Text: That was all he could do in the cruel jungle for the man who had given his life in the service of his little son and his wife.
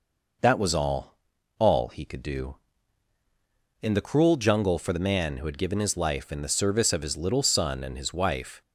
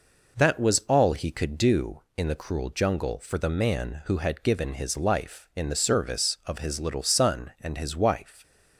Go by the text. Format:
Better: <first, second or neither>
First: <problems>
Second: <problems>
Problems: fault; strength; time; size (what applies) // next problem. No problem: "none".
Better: second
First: says "all" twice; at 1.5 s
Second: none